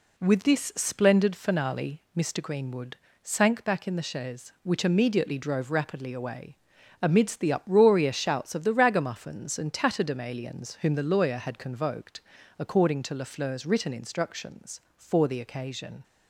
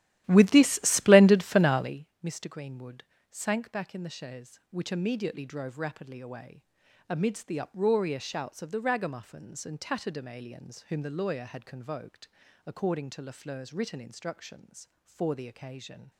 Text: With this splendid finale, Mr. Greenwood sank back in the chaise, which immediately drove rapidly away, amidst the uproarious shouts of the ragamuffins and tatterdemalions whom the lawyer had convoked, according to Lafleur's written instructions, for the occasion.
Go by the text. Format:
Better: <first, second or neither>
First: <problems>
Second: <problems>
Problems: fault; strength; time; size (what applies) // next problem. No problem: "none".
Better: first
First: pauses between "Greenwood" and "sank"; slight; at 2.9 s; 0.26 s long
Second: starts louder than the rest; strong; until 1.9 s; 13.5 dB // pauses between "Greenwood" and "sank"; slight; at 3.0 s; 0.26 s long